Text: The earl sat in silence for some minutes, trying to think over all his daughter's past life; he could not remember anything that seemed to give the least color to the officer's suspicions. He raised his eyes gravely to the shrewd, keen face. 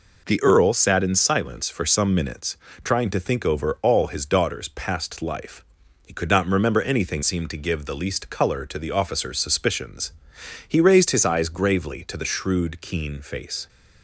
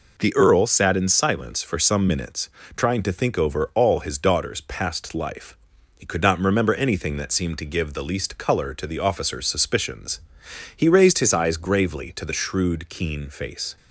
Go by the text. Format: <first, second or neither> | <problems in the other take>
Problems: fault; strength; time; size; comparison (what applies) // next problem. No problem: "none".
second | skips "that"; at 7.2 s